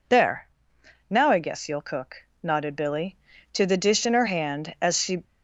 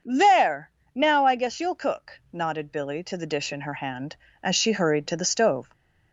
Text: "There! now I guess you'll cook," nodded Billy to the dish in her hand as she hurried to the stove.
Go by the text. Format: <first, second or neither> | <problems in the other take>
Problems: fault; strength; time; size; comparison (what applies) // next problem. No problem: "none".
second | stops before "hurried to the stove"; at 5.2 s